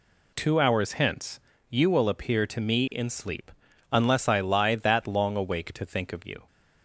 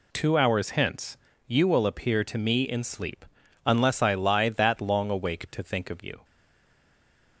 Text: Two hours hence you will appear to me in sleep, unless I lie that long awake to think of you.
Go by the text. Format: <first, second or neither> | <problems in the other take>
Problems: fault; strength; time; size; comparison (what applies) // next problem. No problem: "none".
first | pauses between "hence" and "you"; slight; at 1.1 s; 0.30 s long; slight in the first // stays silent after the last word; noticeable; from 6.2 s on; 1.1 s long